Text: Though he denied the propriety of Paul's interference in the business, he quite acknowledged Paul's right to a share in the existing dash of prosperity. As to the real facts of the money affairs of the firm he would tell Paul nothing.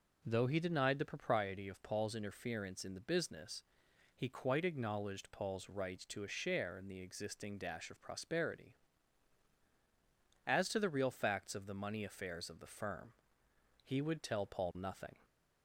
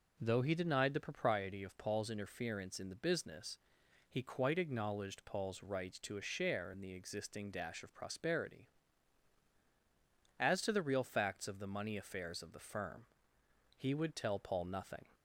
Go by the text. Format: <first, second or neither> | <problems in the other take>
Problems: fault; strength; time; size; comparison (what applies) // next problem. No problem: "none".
neither | pauses between "firm" and "he"; noticeable; the same in both